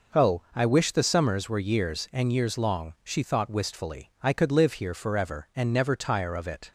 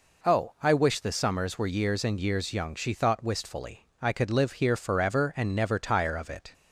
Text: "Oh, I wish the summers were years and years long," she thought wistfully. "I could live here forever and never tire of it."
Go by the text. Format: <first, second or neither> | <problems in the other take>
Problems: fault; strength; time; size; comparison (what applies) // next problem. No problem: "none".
first | says "young" for "long"; at 2.5 s